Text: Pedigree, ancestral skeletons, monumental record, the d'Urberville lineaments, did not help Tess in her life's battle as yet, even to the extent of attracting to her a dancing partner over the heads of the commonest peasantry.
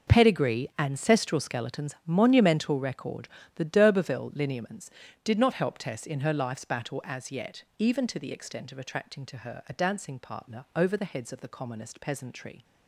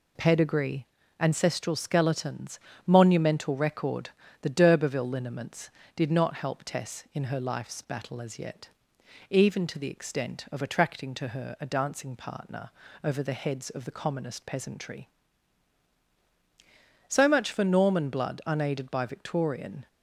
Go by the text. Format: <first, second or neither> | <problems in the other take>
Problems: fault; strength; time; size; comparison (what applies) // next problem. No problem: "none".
first | pauses between "partner" and "over"; slight; at 12.7 s; 0.32 s long // goes on to say "So much for Norman blood unaided by Victorian"; strong; from 17.0 s on; 2.8 s long